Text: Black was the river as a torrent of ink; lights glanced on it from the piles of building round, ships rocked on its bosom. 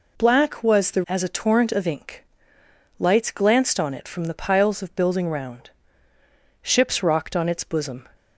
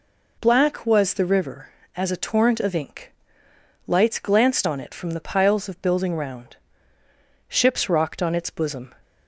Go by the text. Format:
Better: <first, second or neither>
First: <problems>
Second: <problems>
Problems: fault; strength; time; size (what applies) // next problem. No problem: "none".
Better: second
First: skips "river"; at 1.0 s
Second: none